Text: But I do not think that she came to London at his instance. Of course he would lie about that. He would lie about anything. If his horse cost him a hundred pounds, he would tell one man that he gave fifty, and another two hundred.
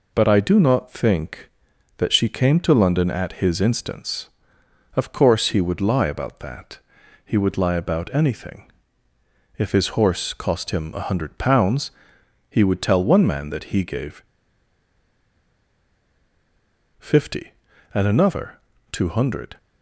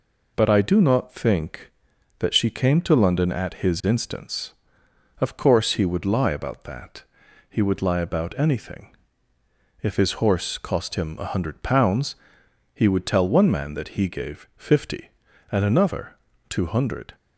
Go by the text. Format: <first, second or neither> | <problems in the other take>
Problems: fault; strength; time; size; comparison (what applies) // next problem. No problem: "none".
second | pauses between "gave" and "fifty"; strong; at 14.2 s; 2.7 s long // pauses between "another" and "two"; slight; at 18.5 s; 0.34 s long; slight in the second